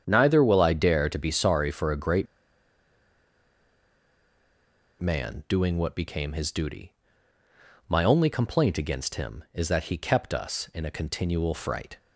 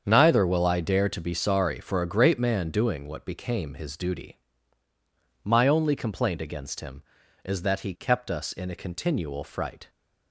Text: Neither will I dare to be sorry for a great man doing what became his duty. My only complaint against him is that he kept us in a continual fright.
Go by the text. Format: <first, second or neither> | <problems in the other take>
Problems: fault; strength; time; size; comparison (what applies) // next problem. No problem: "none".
second | starts louder than the rest; strong; until 1.0 s; 8.5 dB; strong in the second // pauses between "great" and "man"; strong; at 2.2 s; 2.7 s long